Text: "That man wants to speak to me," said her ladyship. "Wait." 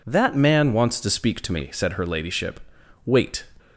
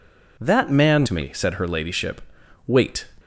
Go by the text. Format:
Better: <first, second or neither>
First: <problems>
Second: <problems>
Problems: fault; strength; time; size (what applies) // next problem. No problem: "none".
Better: first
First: none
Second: skips "wants to speak"; at 1.0 s